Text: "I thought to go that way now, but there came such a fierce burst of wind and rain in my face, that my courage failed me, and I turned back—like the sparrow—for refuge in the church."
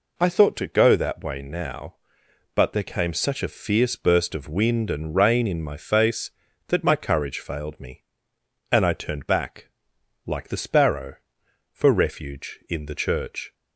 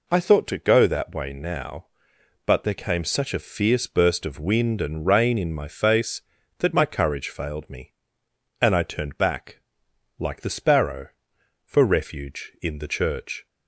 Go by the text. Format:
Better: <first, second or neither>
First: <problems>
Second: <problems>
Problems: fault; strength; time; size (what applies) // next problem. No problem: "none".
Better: neither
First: none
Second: none